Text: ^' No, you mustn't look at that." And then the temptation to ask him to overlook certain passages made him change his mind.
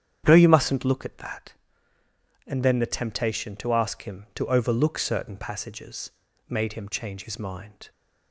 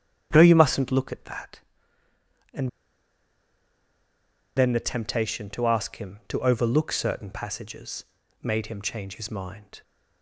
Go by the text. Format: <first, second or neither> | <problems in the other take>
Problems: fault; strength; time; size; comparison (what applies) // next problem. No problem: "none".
first | starts louder than the rest; strong; until 1.3 s; 9 dB; strong in the first // pauses between "And" and "then"; strong; at 2.6 s; 1.8 s long // pauses between "passages" and "made"; at 8.0 s; 0.40 s long; also in the first